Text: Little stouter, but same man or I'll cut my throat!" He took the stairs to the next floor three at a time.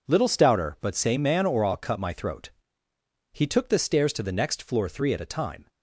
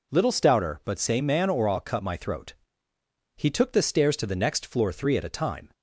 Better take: second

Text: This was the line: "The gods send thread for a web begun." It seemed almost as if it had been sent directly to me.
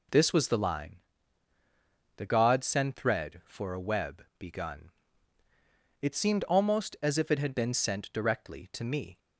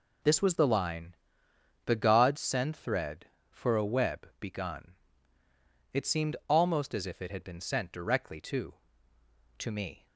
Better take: first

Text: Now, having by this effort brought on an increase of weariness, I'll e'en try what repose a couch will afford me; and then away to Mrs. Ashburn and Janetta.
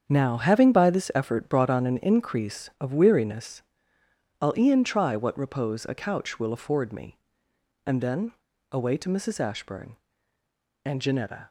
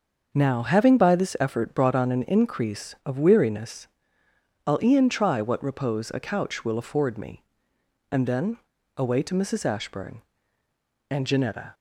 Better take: second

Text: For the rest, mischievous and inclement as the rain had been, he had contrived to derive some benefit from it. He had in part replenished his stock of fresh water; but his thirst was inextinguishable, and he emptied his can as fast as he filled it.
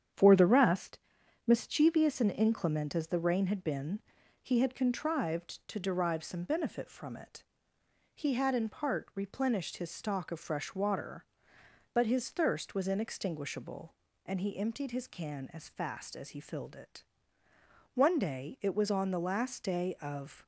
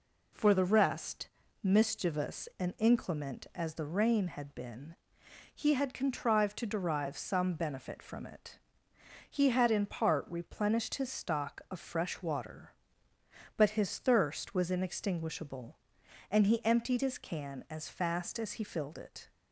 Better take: second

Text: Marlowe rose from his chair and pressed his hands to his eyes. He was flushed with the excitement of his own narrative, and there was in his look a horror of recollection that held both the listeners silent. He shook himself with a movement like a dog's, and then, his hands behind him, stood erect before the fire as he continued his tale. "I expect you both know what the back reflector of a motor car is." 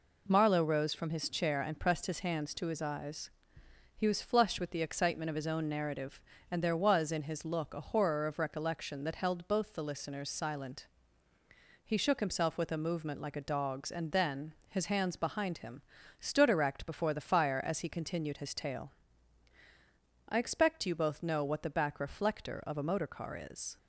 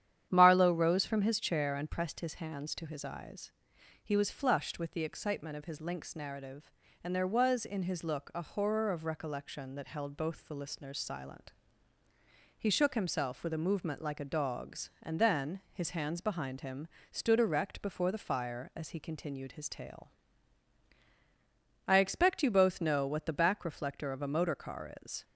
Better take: first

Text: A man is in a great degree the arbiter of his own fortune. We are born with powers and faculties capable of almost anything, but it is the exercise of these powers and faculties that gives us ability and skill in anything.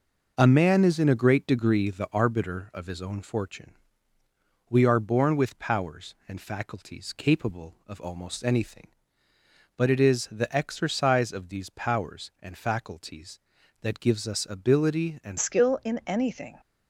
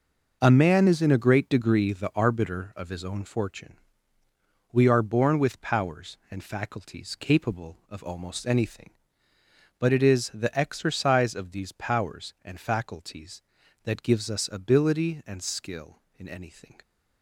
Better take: second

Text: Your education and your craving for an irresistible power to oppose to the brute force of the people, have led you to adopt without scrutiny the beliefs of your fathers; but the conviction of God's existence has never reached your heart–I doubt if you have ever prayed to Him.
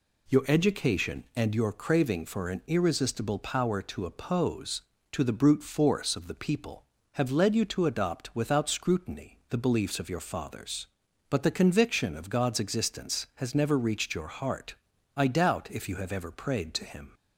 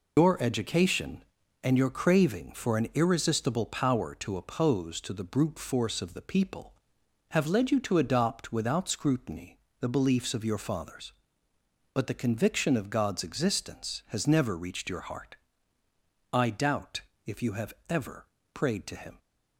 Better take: first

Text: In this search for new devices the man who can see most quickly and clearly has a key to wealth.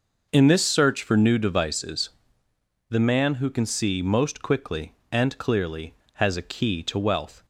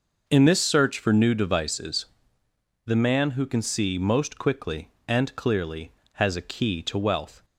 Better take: neither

